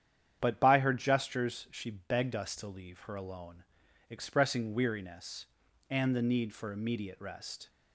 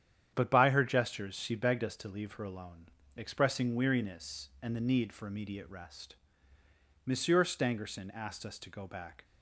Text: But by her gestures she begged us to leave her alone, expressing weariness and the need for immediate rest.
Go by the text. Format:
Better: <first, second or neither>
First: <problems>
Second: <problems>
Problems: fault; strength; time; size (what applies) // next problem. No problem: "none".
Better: first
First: starts louder than the rest; strong; until 1.4 s; 9 dB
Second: starts louder than the rest; strong; until 1.3 s; 9.5 dB // goes on to say "Monsieur Stangerson asked us to go back"; strong; from 7.0 s on; 2.1 s long